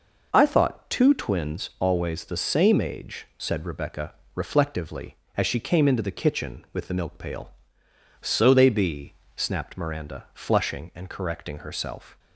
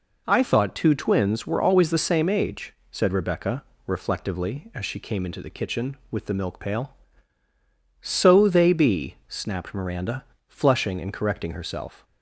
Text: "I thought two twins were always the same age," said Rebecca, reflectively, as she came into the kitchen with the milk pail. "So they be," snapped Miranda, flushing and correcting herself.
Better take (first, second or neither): second